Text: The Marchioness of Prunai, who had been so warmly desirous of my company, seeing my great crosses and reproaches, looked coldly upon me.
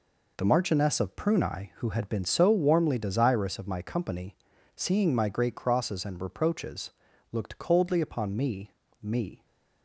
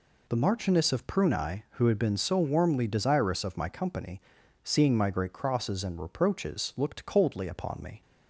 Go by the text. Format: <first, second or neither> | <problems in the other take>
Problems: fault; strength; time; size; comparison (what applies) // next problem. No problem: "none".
second | says "me" twice; at 9.0 s